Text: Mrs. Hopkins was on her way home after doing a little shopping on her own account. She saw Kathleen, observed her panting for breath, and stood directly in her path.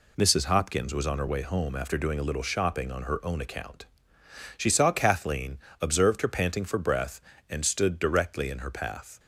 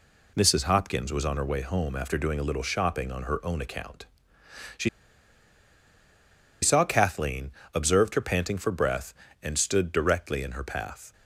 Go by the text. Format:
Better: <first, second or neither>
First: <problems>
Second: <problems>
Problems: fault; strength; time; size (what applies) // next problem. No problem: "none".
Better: first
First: none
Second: pauses between "She" and "saw"; strong; at 4.8 s; 1.7 s long